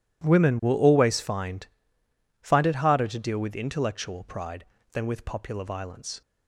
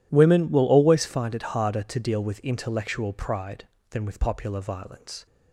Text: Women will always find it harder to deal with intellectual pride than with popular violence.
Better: second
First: says "find" twice; at 2.4 s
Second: none

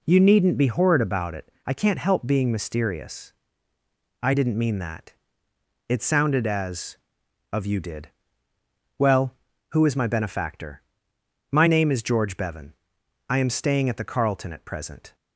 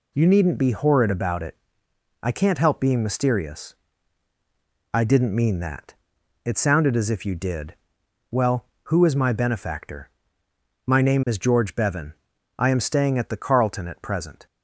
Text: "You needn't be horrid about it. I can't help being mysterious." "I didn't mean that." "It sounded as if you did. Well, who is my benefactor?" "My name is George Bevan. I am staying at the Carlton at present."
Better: second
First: says "of" for "if"; at 7.5 s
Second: none

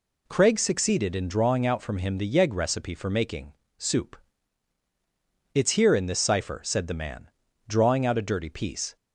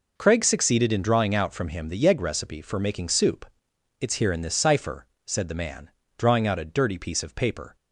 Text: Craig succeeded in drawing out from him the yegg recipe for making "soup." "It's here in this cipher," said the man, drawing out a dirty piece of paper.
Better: second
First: pauses between "making" and "soup"; slight; at 3.5 s; 0.24 s long // stops before "of paper"; at 8.9 s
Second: none

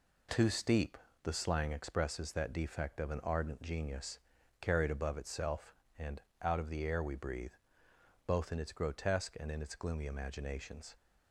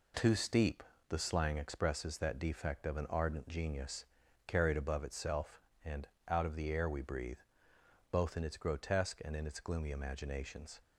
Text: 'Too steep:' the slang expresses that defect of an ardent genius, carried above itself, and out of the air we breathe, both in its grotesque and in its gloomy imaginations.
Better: neither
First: pauses between "and" and "out"; slight; at 6.2 s; 0.22 s long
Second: pauses between "and" and "out"; slight; at 6.0 s; 0.22 s long

